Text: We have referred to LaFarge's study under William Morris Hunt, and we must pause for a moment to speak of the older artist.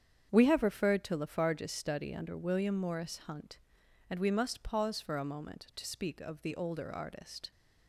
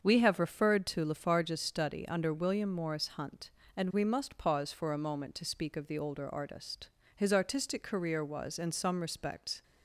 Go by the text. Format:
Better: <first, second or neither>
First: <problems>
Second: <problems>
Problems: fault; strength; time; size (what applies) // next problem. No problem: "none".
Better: first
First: starts louder than the rest; strong; until 1.3 s; 8 dB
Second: starts louder than the rest; until 1.0 s; 7 dB // goes on to say "His artistic career was in some respects"; strong; from 7.1 s on; 2.4 s long